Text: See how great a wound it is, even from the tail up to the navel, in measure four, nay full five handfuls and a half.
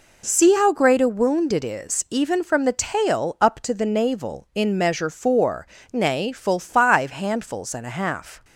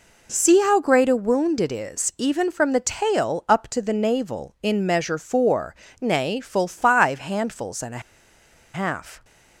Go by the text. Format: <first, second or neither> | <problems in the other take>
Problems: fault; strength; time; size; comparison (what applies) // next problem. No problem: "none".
first | pauses between "a" and "half"; noticeable; at 8.0 s; 0.74 s long